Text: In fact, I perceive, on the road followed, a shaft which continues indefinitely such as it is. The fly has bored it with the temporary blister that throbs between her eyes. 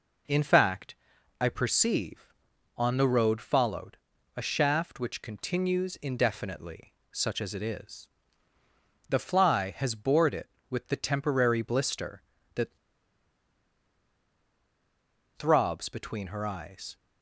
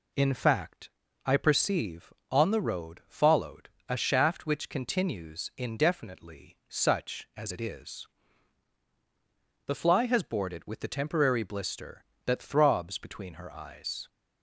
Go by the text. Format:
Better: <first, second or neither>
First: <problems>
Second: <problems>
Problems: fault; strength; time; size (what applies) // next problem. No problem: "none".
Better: second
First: pauses between "indefinitely" and "such"; slight; at 6.9 s; 0.18 s long // pauses between "that" and "throbs"; strong; at 12.7 s; 2.5 s long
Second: none